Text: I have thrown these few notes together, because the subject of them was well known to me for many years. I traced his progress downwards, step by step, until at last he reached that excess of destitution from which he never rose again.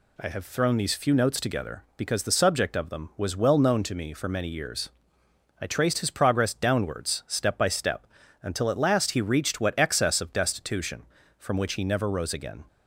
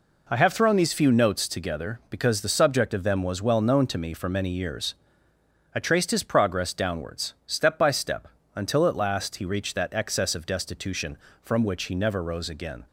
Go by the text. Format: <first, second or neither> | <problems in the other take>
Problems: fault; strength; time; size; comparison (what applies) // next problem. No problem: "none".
second | says "what" for "that"; at 9.5 s